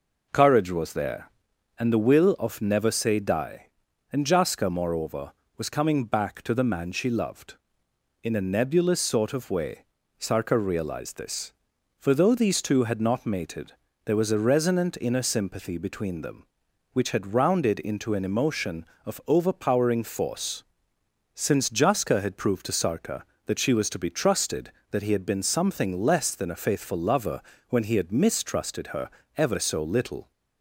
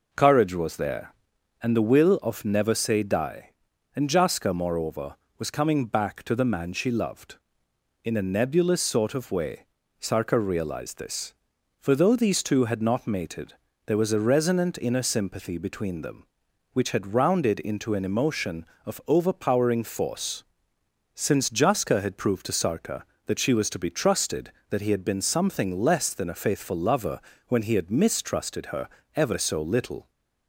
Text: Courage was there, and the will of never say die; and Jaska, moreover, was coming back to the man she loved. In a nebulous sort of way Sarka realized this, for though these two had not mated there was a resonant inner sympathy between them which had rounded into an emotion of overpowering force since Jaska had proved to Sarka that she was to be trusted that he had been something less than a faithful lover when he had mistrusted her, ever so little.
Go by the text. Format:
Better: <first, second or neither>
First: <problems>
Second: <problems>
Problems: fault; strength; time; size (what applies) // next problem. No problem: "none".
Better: neither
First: pauses between "way" and "Sarka"; slight; at 9.8 s; 0.34 s long // pauses between "mated" and "there"; slight; at 13.7 s; 0.32 s long // pauses between "force" and "since"; noticeable; at 20.6 s; 0.72 s long // pauses between "lover" and "when"; slight; at 27.4 s; 0.28 s long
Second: pauses between "way" and "Sarka"; slight; at 9.6 s; 0.34 s long // pauses between "mated" and "there"; slight; at 13.5 s; 0.32 s long // pauses between "force" and "since"; noticeable; at 20.4 s; 0.72 s long // pauses between "lover" and "when"; slight; at 27.1 s; 0.28 s long